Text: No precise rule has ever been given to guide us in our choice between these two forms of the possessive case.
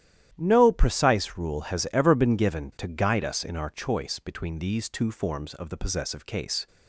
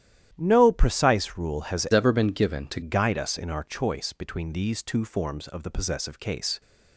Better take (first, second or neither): first